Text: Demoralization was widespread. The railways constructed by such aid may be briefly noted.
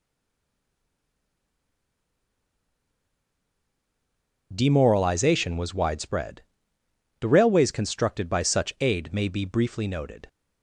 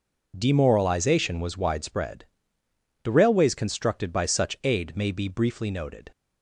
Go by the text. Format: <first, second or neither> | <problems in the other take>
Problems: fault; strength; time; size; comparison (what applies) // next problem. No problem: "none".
second | stays silent before the first word; strong; until 4.5 s; 4.5 s long